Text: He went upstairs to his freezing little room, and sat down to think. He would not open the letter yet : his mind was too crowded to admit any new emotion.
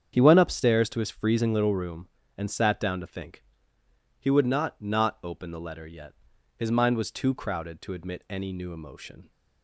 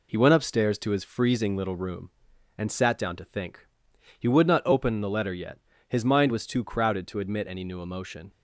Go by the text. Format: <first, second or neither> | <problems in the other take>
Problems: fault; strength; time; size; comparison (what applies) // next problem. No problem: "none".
second | starts louder than the rest; strong; until 1.1 s; 8 dB // says "not" twice; at 4.7 s